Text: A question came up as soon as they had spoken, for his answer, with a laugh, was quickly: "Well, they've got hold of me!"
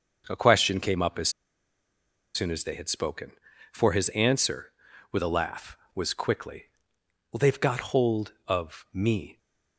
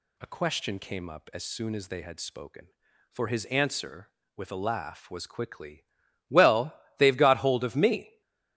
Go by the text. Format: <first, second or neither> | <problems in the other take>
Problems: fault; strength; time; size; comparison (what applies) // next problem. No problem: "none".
second | starts louder than the rest; noticeable; until 1.2 s; 6 dB // pauses between "as" and "soon"; at 1.2 s; 1.0 s long